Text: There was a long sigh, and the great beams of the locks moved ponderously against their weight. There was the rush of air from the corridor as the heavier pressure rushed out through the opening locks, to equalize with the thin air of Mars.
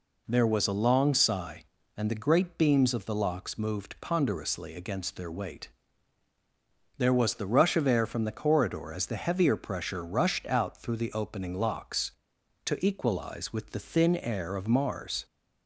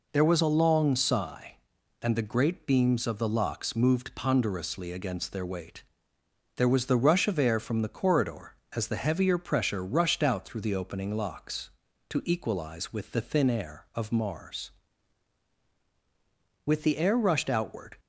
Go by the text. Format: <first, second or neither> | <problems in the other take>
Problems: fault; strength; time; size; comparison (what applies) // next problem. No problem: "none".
first | goes on to say "With the air rushed outward"; from 16.6 s on; 1.3 s long